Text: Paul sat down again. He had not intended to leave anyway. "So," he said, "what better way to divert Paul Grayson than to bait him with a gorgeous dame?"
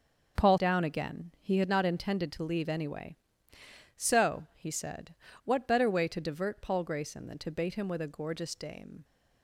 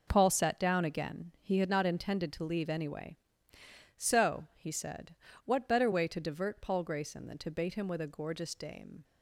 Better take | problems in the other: second | starts louder than the rest; noticeable; until 1.4 s; 6 dB // skips "sat"; at 0.5 s

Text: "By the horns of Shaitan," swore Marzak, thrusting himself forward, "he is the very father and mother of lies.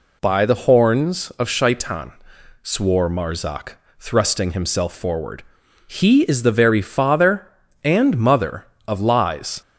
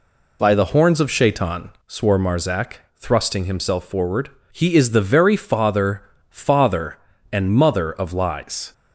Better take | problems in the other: first | says "father" twice; at 6.3 s

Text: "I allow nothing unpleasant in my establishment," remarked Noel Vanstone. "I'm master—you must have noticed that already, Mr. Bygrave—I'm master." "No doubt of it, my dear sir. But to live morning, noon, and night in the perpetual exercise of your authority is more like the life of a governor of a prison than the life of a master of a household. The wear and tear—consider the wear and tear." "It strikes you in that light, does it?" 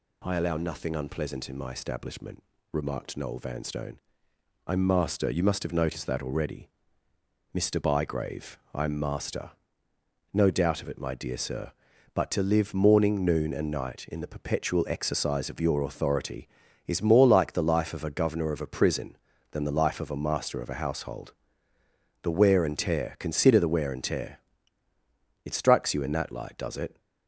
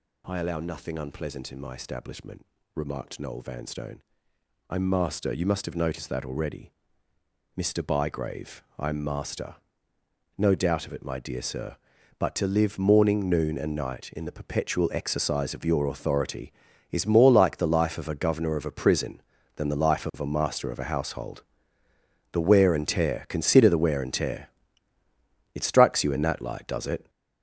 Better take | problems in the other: first | gets louder; strong; throughout; 7.5 dB

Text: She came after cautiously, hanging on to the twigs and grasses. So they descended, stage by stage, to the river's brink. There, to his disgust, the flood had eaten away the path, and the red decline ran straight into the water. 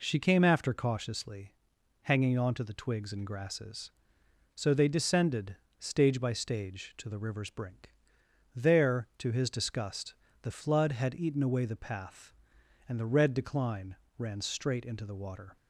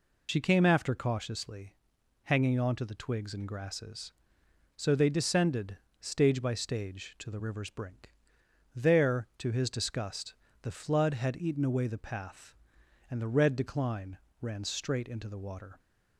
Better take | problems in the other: first | loses the start of "She"; at 0.2 s; 75 ms // pauses between "decline" and "ran"; slight; at 14.1 s; 0.24 s long; slight in the first

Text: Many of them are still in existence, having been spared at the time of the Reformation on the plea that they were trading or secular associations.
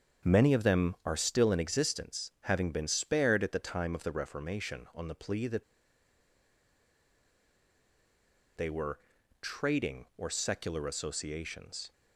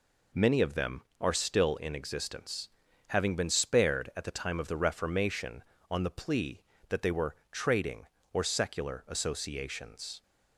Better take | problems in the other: second | starts louder than the rest; strong; until 1.3 s; 7.5 dB // pauses between "that" and "they"; strong; at 5.6 s; 2.9 s long // pauses between "were" and "trading"; at 8.9 s; 0.42 s long; slight in the second

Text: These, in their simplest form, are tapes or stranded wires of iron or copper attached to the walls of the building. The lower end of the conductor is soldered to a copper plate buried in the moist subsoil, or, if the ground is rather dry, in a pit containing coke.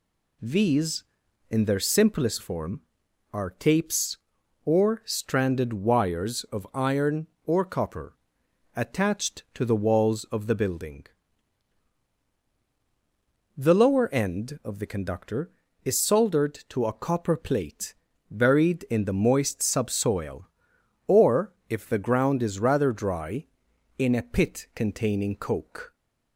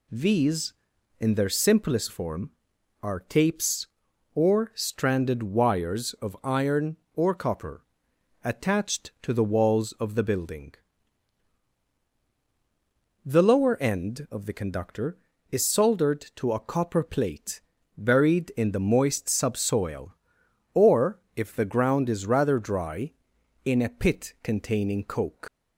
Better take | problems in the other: first | pauses between "copper" and "attached"; noticeable; at 7.8 s; 0.60 s long; noticeable in the first // pauses between "plate" and "buried"; slight; at 17.6 s; 0.34 s long; slight in the first // leaves "coke" unfinished; at 25.4 s; 155 ms

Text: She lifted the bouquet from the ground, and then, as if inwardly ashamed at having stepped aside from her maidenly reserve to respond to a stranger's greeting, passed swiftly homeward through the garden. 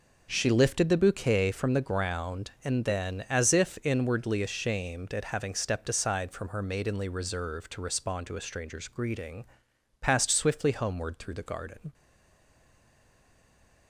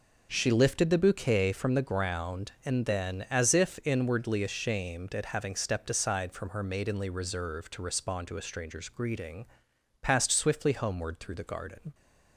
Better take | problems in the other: second | stays silent after the last word; noticeable; from 11.9 s on; 1.9 s long

